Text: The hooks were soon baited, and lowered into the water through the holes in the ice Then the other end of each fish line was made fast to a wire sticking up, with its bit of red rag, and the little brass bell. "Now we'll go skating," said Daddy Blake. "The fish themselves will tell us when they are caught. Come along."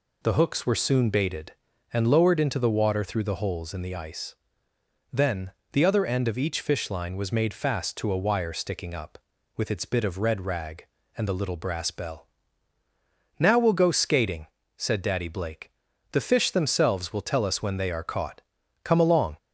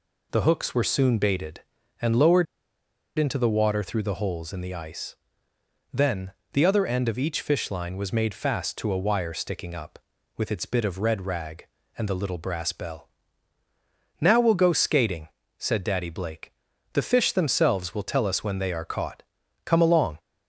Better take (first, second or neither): first